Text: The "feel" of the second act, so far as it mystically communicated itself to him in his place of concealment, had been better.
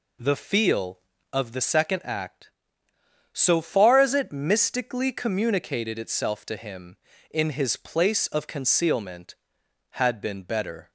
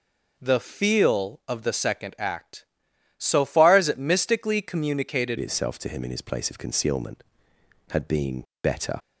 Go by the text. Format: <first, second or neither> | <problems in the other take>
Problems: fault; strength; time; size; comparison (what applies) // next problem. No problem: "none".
first | changes voice at "itself"; from 5.3 s on; 3.6 s long // pauses between "been" and "better"; slight; at 8.4 s; 0.18 s long